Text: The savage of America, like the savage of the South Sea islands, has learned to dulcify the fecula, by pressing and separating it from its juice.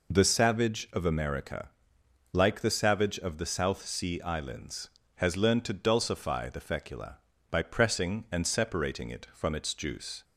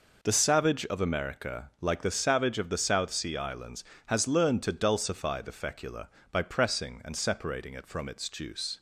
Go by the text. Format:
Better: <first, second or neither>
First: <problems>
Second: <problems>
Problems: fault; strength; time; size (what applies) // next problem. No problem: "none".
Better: neither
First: none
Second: none